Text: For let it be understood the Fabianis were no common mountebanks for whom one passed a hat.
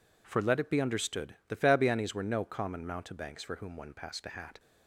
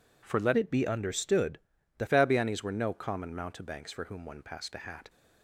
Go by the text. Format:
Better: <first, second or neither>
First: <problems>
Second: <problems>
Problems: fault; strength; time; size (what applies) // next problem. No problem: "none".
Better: first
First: none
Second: changes voice from "it" to "the"; from 0.5 to 2.0 s; 1.5 s long // pauses between "understood" and "the"; at 1.6 s; 0.38 s long